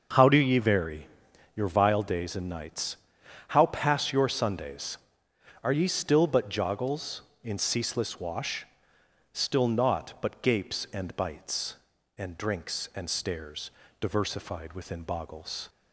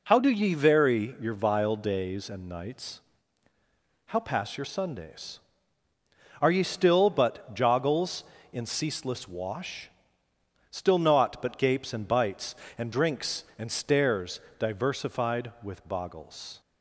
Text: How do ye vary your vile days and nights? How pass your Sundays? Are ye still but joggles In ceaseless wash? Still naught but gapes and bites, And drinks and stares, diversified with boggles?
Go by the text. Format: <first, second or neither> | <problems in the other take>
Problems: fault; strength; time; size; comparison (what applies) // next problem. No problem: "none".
second | starts louder than the rest; until 1.6 s; 6 dB // pauses between "vary" and "your"; noticeable; at 1.0 s; 0.48 s long // says "within" for "with"; at 14.7 s